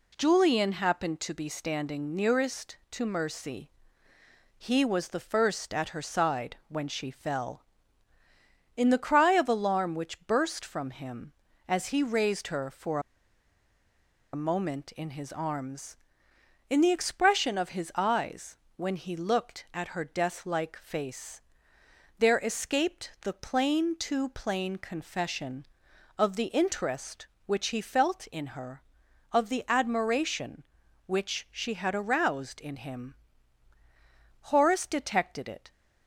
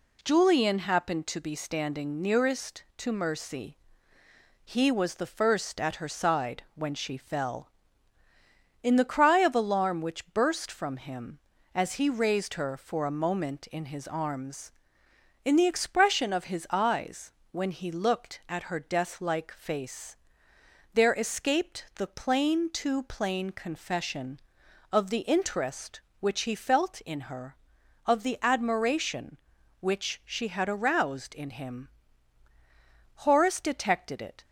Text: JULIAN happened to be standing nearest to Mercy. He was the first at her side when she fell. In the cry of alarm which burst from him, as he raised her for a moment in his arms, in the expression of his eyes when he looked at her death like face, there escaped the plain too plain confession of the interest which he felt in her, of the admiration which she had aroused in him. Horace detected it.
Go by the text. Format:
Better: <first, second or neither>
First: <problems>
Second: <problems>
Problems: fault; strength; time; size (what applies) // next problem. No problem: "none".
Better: second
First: pauses between "for" and "a"; strong; at 12.9 s; 1.3 s long // pauses between "eyes" and "when"; slight; at 18.5 s; 0.20 s long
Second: pauses between "eyes" and "when"; slight; at 17.3 s; 0.20 s long